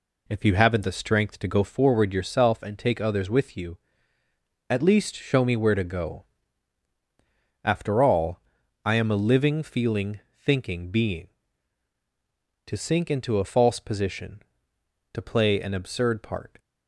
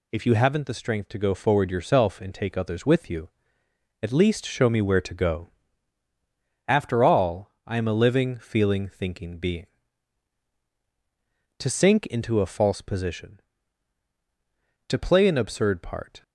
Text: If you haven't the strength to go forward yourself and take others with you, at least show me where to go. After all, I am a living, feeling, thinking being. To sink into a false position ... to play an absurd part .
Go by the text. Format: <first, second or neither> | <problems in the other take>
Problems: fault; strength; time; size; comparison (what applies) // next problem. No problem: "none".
second | starts louder than the rest; slight; until 1.7 s; 3 dB